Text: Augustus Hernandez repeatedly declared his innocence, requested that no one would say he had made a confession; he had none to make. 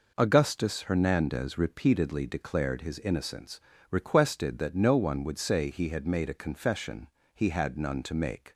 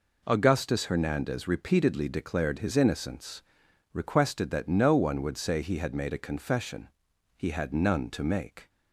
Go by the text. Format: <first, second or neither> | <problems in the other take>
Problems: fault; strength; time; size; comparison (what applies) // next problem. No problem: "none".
neither | none